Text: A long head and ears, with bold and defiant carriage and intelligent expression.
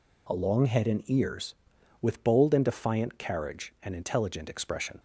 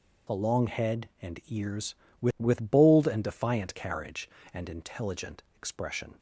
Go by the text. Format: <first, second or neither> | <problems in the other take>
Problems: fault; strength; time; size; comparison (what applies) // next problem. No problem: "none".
first | says "with" twice; at 2.3 s